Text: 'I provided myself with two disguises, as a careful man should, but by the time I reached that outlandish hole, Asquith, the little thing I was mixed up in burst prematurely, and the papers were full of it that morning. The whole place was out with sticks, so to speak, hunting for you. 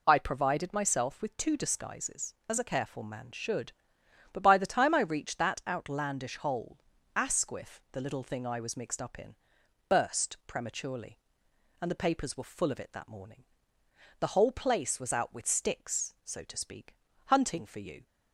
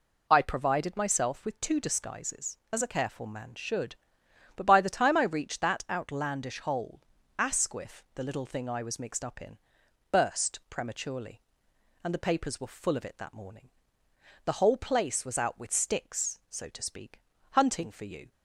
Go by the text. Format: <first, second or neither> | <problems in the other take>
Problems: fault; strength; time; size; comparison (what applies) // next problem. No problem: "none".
neither | pauses between "in" and "burst"; noticeable; the same in both